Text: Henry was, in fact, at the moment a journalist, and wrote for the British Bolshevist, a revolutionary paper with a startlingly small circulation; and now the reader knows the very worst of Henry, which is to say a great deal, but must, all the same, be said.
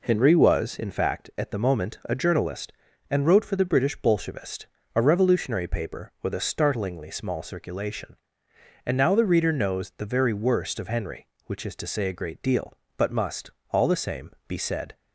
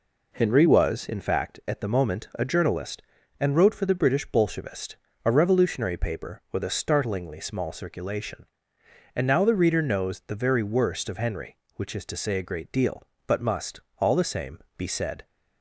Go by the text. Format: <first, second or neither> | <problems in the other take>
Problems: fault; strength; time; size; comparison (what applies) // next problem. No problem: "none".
neither | none